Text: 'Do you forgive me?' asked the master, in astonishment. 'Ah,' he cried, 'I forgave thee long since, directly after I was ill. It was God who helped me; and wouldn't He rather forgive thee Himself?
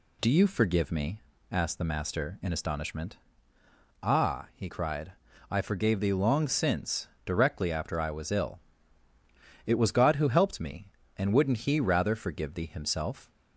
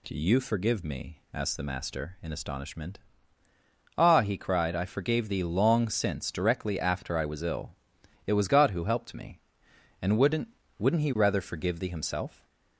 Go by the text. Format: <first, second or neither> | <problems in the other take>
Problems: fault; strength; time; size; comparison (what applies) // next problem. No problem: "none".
first | says "wouldn't" twice; at 10.7 s